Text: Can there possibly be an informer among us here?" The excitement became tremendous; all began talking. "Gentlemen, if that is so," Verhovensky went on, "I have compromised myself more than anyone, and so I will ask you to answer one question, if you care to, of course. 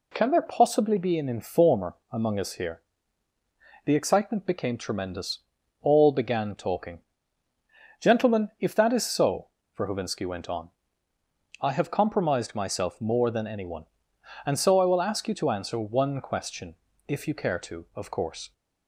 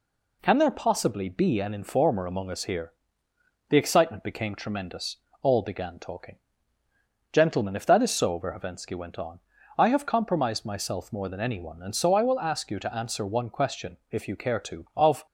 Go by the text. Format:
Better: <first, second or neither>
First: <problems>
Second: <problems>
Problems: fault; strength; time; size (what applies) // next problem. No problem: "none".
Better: first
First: none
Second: stops before "course"; at 15.2 s